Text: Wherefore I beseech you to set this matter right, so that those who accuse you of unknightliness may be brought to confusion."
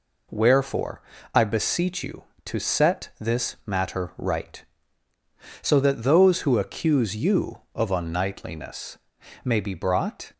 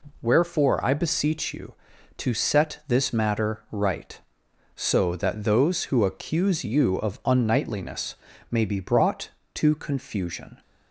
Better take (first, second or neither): second